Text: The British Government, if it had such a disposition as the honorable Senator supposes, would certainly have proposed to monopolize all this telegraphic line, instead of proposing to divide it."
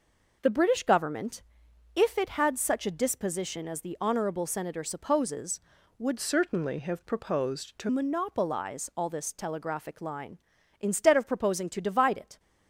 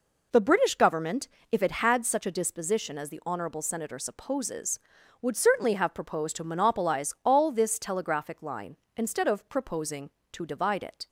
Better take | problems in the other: second | changes voice from "certainly" to "to"; from 6.1 to 7.8 s; 1.7 s long

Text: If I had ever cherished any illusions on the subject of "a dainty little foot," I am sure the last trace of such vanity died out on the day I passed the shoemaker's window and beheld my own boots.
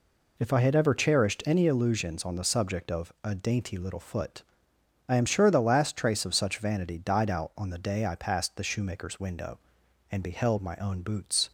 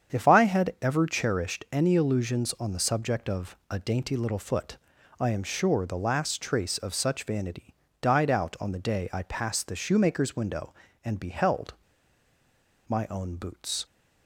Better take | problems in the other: first | starts louder than the rest; strong; until 1.1 s; 8 dB // pauses between "vanity" and "died"; slight; at 7.7 s; 0.26 s long // pauses between "beheld" and "my"; at 11.7 s; 1.1 s long

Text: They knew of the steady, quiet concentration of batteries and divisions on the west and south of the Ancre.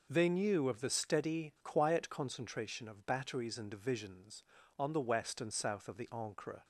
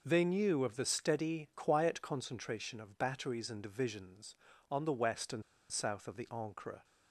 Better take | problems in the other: first | pauses between "and" and "south"; slight; at 5.4 s; 0.27 s long

